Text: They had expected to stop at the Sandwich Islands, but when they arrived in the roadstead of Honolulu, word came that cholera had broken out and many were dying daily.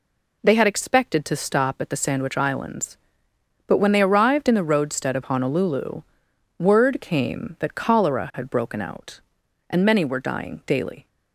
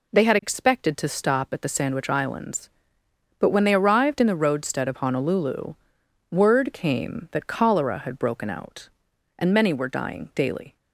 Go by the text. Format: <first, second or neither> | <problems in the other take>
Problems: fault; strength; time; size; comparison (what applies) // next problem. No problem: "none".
neither | none